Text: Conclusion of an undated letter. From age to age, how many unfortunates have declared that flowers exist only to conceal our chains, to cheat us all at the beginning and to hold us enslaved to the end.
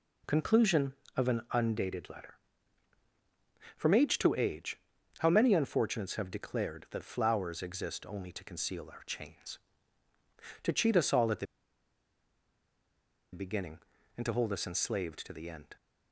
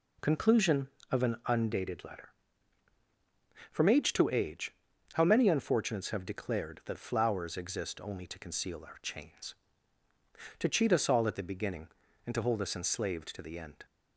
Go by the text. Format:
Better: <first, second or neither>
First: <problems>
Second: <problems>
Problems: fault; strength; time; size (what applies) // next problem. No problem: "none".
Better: second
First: pauses between "the" and "beginning"; strong; at 11.4 s; 1.8 s long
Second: none